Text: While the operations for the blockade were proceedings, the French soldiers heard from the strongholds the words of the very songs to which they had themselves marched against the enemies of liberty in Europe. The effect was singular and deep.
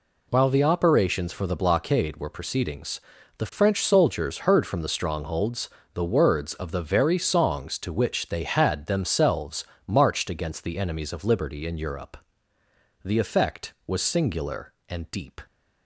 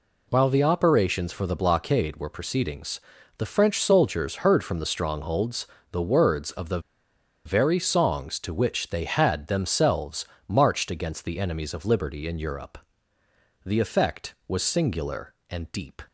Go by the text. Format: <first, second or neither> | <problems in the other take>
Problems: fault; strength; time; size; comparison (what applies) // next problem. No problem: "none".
first | pauses between "strongholds" and "the"; slight; at 5.6 s; 0.26 s long; slight in the first // pauses between "the" and "very"; noticeable; at 6.7 s; 0.66 s long // pauses between "themselves" and "marched"; slight; at 10.2 s; 0.20 s long; slight in the first